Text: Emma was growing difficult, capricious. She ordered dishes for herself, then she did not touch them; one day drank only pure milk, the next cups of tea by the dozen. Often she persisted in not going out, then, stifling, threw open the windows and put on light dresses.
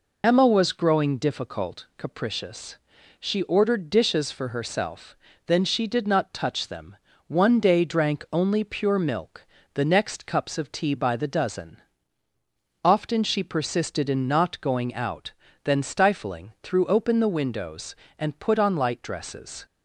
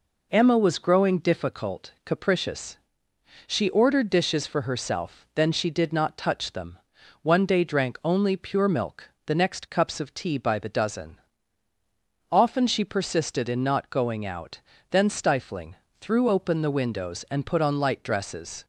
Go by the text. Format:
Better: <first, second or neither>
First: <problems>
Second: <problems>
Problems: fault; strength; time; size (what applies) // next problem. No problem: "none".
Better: second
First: loses the start of "Emma"; at 0.2 s; 30 ms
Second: none